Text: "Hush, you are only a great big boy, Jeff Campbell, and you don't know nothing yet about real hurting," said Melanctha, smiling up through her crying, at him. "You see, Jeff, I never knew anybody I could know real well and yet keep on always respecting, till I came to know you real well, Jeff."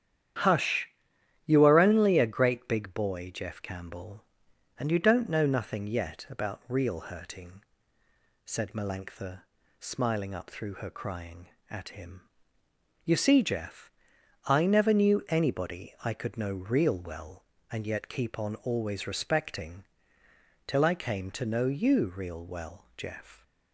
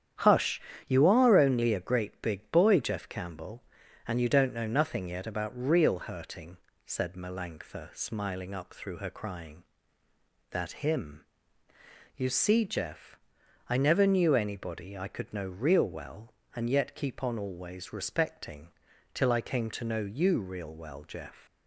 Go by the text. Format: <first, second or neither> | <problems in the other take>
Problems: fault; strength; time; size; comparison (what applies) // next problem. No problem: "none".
first | starts louder than the rest; strong; until 1.5 s; 9.5 dB; strong in the first // says "that" for "at"; at 10.4 s